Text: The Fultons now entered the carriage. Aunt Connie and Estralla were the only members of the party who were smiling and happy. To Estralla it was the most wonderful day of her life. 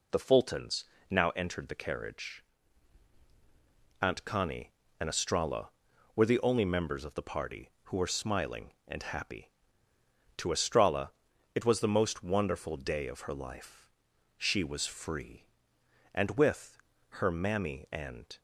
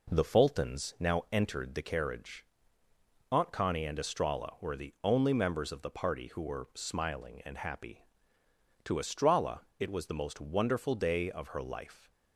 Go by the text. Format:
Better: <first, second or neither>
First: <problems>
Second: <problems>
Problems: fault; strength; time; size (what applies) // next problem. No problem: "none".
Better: second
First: pauses between "Fultons" and "now"; slight; at 0.8 s; 0.24 s long // pauses between "Estralla" and "it"; at 11.1 s; 0.42 s long // goes on to say "She was free And with her mammy and"; strong; from 14.3 s on; 4.0 s long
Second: none